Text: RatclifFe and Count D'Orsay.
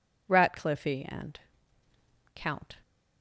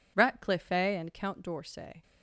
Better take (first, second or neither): second